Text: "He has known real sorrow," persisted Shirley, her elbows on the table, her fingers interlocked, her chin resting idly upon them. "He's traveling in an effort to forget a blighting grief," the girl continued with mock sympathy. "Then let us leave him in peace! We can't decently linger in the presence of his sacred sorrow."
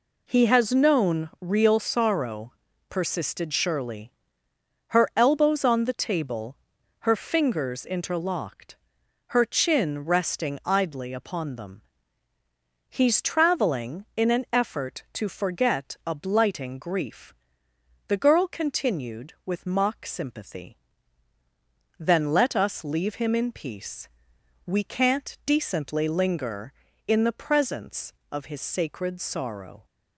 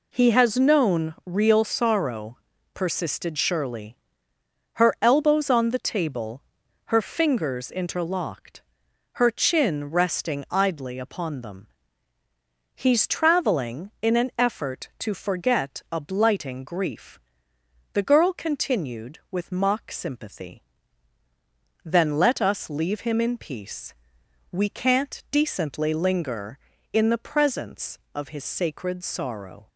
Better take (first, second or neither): neither